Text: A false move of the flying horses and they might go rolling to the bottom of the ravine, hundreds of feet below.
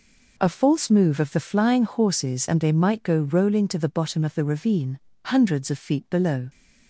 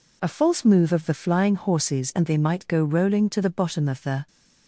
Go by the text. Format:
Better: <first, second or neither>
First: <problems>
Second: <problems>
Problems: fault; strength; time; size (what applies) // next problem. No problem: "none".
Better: first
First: none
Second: stops before "ravine hundreds of feet below"; at 4.2 s